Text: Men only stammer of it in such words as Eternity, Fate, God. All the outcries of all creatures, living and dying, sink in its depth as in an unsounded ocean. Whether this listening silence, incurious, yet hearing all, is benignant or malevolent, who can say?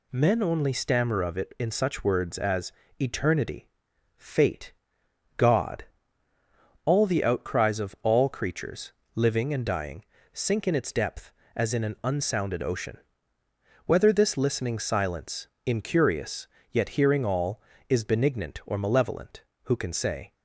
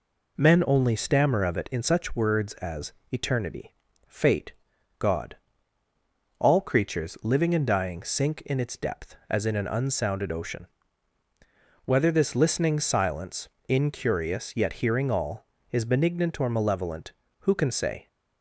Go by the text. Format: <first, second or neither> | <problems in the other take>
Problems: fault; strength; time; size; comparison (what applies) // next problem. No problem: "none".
first | pauses between "as" and "Eternity"; slight; at 2.9 s; 0.18 s long; slight in the first // skips "the outcries of all"; at 6.5 s